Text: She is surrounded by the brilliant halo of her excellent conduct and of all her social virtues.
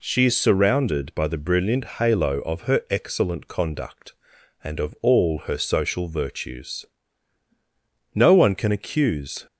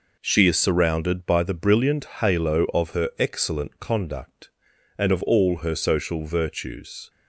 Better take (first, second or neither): second